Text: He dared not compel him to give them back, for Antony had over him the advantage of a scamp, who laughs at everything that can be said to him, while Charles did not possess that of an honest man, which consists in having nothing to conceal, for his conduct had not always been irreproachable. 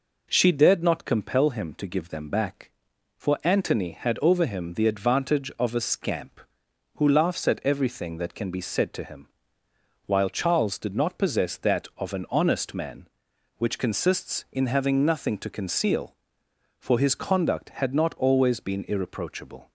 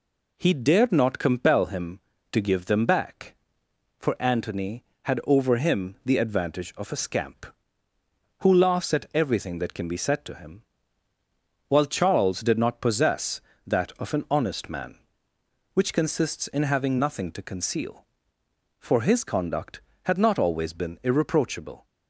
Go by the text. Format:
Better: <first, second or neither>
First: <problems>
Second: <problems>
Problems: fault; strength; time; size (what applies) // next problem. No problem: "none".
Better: second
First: says "She" for "He"; at 0.2 s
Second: none